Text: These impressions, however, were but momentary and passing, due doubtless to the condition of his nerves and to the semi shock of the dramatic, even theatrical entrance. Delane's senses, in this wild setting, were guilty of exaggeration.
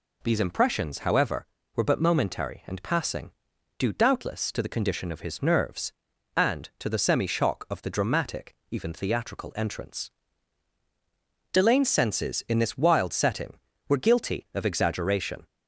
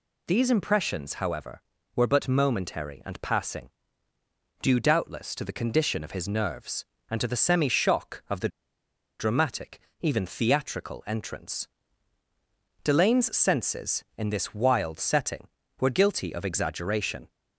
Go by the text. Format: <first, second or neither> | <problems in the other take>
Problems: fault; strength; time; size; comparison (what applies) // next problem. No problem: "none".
first | pauses between "the" and "dramatic"; noticeable; at 8.4 s; 0.70 s long